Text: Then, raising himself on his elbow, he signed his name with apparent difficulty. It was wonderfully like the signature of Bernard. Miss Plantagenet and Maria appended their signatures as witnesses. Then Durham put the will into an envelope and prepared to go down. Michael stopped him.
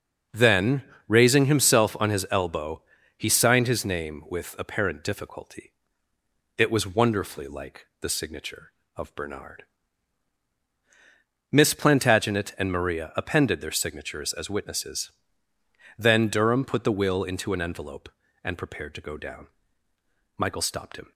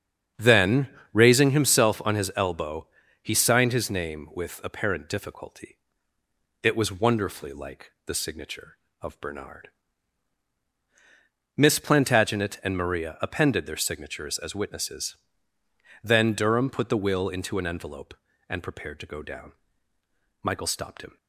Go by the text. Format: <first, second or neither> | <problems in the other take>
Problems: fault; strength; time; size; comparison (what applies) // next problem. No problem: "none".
first | starts louder than the rest; strong; until 1.5 s; 7.5 dB